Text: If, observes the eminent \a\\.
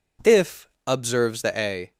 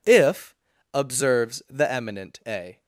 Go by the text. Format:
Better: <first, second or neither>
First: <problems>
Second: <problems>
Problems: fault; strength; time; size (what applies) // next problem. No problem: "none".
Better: second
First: skips "eminent"; at 1.5 s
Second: none